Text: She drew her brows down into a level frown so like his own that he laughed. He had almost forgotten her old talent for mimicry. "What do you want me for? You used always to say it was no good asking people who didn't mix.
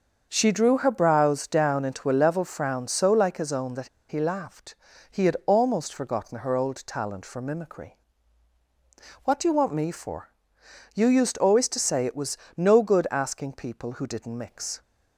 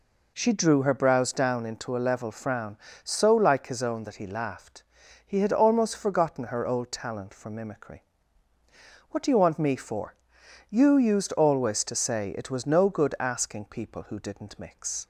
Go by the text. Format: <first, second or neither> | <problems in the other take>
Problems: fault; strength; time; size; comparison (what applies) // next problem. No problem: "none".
second | starts louder than the rest; until 1.3 s; 6.5 dB // pauses between "that" and "he"; slight; at 3.8 s; 0.21 s long // pauses between "was" and "no"; slight; at 12.3 s; 0.22 s long